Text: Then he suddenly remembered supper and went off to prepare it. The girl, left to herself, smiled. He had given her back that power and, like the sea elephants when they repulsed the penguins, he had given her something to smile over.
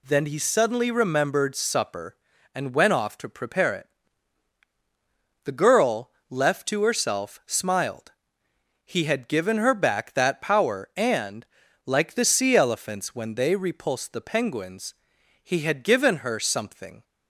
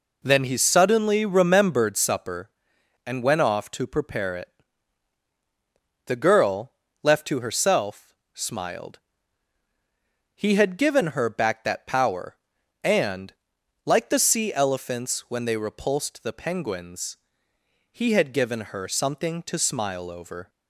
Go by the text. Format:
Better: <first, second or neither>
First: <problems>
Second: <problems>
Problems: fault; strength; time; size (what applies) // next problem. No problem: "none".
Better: second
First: stops before "to smile over"; at 17.0 s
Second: none